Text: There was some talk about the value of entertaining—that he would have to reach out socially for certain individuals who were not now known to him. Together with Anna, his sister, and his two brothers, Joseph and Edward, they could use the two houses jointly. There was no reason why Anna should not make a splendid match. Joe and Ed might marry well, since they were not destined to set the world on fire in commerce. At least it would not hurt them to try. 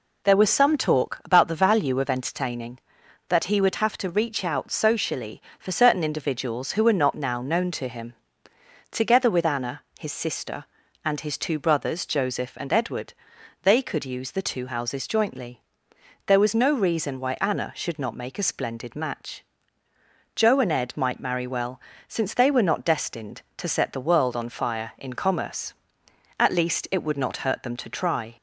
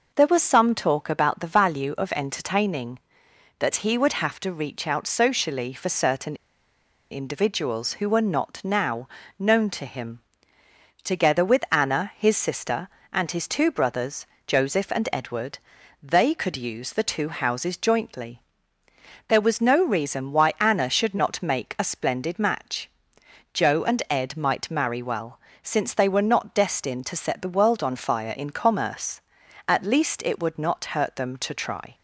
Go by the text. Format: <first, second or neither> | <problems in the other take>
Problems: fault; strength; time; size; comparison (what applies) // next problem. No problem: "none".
first | pauses between "certain" and "individuals"; noticeable; at 6.3 s; 0.74 s long // pauses between "now" and "known"; slight; at 9.0 s; 0.28 s long